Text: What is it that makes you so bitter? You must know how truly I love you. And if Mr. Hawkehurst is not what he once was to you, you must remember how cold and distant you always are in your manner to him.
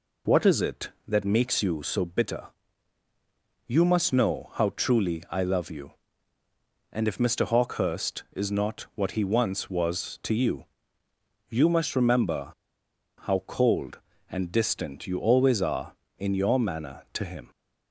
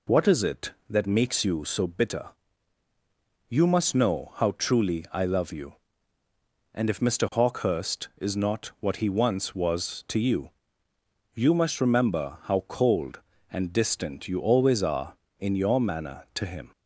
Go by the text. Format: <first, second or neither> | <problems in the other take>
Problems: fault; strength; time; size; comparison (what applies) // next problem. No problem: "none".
second | pauses between "remember" and "how"; noticeable; at 12.5 s; 0.68 s long